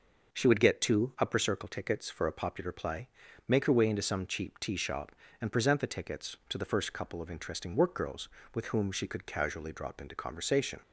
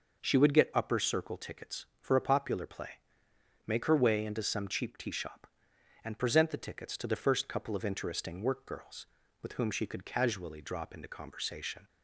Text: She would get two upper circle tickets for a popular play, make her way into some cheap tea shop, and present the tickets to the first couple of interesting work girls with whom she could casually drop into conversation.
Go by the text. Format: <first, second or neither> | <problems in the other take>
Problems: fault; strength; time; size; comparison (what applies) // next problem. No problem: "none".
first | skips "two"; at 0.7 s